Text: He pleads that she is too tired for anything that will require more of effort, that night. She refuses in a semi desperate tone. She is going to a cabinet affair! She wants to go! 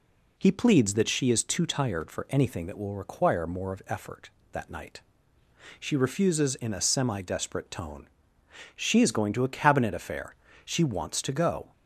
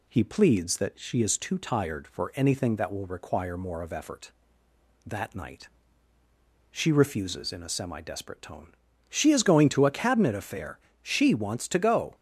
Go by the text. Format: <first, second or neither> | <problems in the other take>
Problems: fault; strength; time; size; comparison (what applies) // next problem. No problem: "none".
neither | none